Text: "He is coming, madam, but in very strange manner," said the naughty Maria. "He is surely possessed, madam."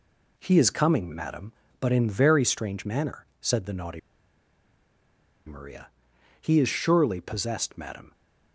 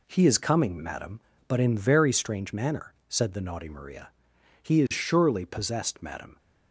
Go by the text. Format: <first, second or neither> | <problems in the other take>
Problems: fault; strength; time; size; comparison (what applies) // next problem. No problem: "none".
second | pauses between "naughty" and "Maria"; strong; at 3.9 s; 1.4 s long